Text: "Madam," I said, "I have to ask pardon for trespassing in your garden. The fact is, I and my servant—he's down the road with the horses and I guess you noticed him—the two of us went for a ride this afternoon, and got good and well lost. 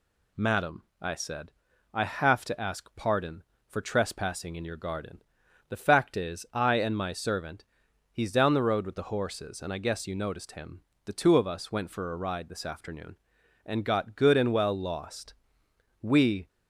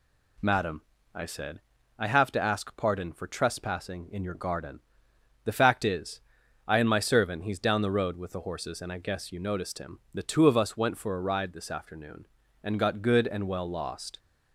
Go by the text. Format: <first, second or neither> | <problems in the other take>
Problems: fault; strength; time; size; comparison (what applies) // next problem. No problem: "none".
second | goes on to say "We"; slight; from 16.0 s on; 0.46 s long